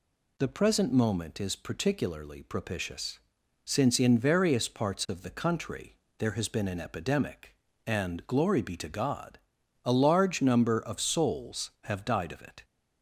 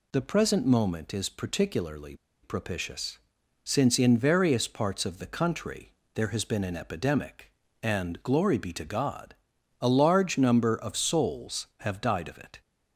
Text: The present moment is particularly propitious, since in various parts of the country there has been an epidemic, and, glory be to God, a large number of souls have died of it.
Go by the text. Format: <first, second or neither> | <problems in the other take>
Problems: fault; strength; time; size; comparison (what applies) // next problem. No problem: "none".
first | pauses between "particularly" and "propitious"; slight; at 2.1 s; 0.28 s long // pauses between "country" and "there"; slight; at 5.9 s; 0.22 s long; slight in the first